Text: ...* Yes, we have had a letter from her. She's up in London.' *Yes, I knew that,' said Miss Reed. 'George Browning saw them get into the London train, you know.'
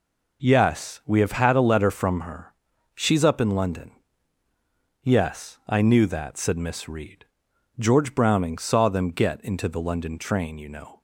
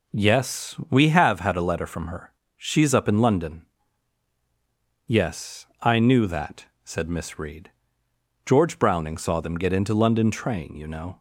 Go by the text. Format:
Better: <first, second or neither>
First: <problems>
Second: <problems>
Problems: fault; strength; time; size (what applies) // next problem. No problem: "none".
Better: first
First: none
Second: skips "the"; at 9.9 s